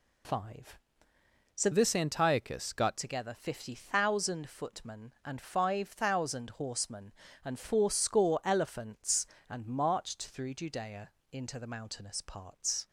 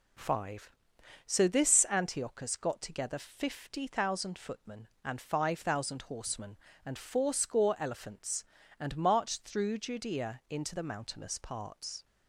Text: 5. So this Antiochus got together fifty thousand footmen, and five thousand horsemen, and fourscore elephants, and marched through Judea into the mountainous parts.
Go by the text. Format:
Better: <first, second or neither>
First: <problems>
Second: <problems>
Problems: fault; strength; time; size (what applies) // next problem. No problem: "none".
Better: second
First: changes voice from "this" to "got"; from 1.7 to 2.9 s; 1.2 s long // pauses between "Judea" and "into"; slight; at 11.1 s; 0.20 s long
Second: none